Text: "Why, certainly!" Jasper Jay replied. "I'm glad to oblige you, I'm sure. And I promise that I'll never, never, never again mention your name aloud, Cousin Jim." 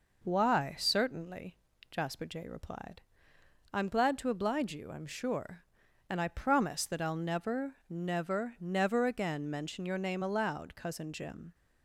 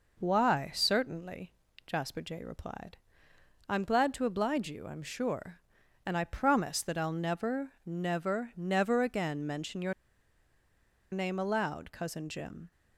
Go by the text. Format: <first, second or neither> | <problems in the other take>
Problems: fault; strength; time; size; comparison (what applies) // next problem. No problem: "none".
first | pauses between "your" and "name"; at 9.9 s; 1.1 s long